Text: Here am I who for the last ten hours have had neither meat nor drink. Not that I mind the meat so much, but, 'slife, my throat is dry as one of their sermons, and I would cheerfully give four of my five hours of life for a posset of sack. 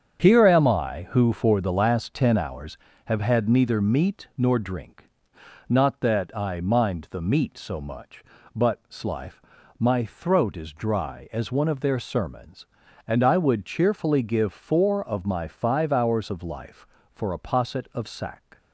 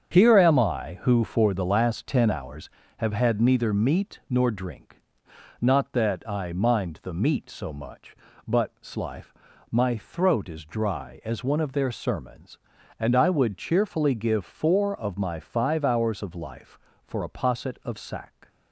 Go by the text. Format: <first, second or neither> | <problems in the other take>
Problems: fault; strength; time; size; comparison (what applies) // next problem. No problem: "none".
neither | starts louder than the rest; strong; the same in both